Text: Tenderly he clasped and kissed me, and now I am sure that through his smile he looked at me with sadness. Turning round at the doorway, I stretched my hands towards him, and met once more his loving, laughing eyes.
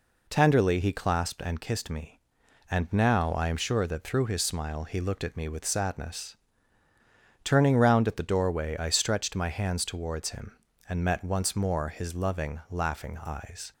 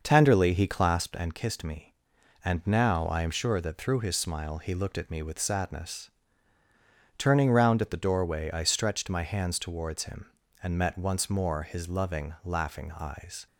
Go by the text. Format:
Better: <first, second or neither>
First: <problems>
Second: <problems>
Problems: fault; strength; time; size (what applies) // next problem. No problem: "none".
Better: first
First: none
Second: starts louder than the rest; noticeable; until 1.2 s; 6 dB